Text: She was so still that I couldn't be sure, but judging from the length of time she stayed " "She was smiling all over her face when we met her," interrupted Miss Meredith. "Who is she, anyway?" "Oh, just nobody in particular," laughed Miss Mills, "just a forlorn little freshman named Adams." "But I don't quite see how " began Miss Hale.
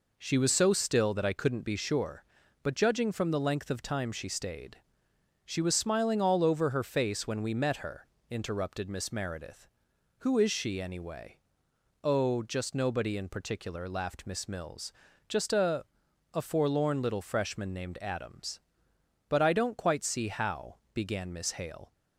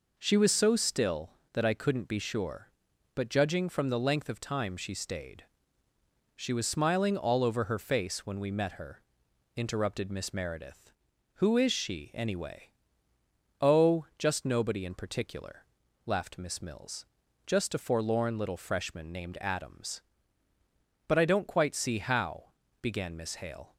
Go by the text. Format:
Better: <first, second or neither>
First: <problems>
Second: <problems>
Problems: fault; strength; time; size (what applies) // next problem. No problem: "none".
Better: second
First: says "a" twice; at 16.3 s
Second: none